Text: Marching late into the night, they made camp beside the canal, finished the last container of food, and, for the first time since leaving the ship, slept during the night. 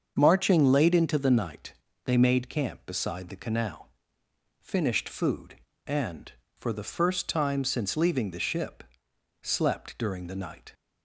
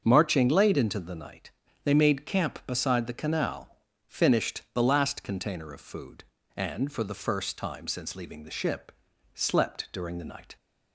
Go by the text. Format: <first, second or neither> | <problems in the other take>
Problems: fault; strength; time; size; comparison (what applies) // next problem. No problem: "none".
second | starts louder than the rest; until 1.1 s; 7 dB; also in the second // skips "the last container of"; at 5.0 s